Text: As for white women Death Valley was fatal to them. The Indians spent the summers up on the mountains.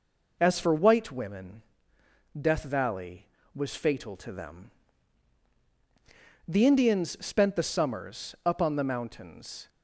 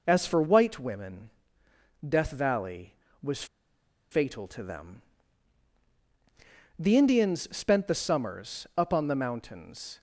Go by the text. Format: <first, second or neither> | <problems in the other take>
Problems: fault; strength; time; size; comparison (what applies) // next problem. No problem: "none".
first | pauses between "women" and "Death"; noticeable; at 1.2 s; 0.78 s long; noticeable in the first // pauses between "was" and "fatal"; noticeable; at 3.4 s; 0.66 s long